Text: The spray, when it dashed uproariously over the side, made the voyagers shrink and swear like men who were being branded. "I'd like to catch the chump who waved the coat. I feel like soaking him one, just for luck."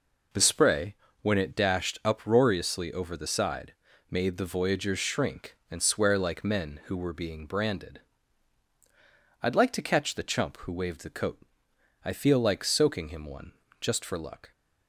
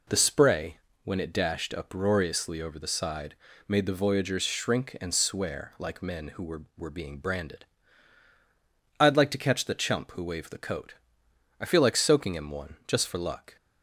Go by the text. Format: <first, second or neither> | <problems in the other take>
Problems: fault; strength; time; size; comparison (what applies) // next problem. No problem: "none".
first | says "were" twice; at 6.7 s